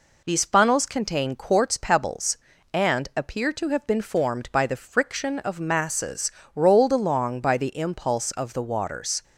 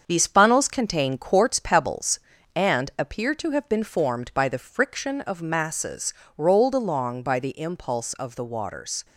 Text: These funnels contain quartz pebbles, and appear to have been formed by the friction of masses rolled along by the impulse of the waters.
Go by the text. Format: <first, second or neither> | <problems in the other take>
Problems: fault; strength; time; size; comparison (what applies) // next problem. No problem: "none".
first | gets quieter; noticeable; throughout; 5 dB // pauses between "masses" and "rolled"; slight; at 6.1 s; 0.24 s long; slight in the first